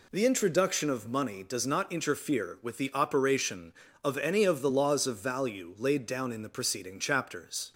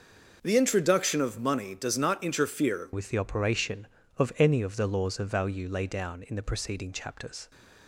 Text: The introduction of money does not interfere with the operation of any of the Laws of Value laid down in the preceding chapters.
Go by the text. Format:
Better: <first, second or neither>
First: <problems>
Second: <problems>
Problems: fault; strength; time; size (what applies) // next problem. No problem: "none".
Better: first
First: none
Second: changes voice at "with"; from 2.9 s on; 4.6 s long